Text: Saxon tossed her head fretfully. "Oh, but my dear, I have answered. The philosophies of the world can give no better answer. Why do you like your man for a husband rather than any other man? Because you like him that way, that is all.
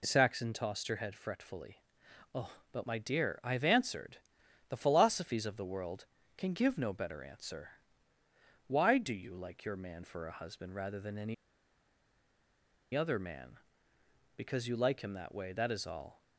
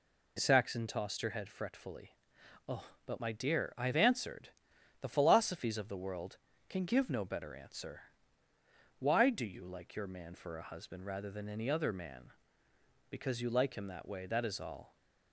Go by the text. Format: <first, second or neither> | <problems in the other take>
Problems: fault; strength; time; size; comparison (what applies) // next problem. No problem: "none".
second | pauses between "any" and "other"; strong; at 11.3 s; 1.6 s long